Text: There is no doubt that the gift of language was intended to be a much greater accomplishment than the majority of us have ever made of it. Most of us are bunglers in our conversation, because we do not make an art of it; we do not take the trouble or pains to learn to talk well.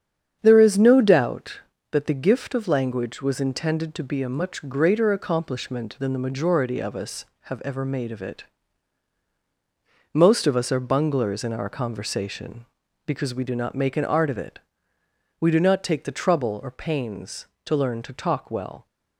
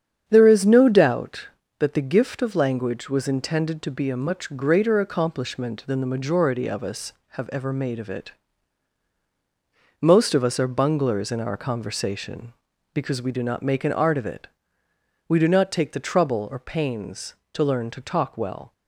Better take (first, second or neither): neither